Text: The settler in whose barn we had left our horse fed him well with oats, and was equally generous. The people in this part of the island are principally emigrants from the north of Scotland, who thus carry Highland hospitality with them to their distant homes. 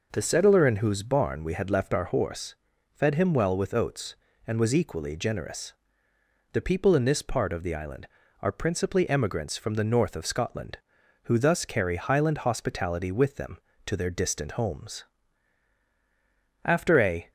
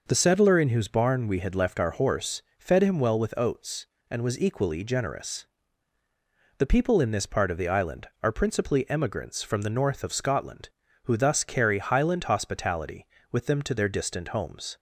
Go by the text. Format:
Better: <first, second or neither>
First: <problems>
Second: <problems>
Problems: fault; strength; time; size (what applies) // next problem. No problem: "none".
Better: second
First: pauses between "horse" and "fed"; at 2.5 s; 0.38 s long // goes on to say "After a"; noticeable; from 16.6 s on; 0.66 s long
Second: pauses between "horse" and "fed"; slight; at 2.4 s; 0.18 s long